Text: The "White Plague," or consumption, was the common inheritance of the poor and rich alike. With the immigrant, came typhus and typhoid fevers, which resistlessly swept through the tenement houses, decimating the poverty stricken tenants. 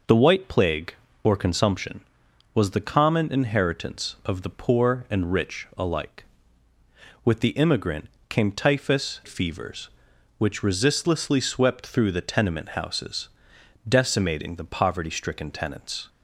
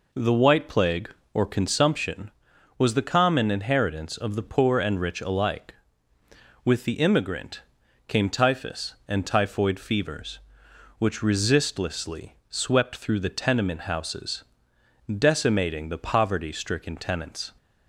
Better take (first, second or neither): second